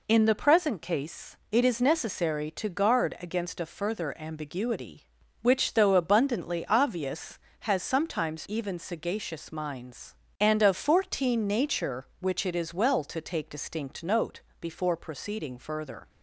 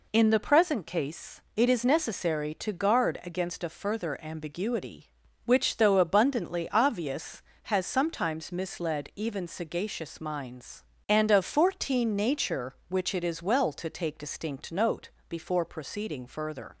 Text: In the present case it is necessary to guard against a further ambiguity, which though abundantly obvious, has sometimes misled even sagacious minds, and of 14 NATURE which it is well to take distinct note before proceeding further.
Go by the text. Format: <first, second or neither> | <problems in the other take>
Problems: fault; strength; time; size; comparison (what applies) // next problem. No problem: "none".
second | skips "misled"; at 8.4 s // pauses between "note" and "before"; slight; at 14.4 s; 0.18 s long; slight in the second